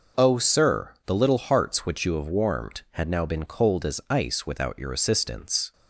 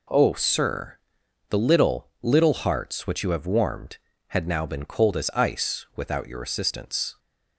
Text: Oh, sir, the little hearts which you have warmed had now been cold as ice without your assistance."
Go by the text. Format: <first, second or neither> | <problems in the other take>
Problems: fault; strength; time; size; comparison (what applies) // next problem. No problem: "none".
first | says "little" twice; at 2.2 s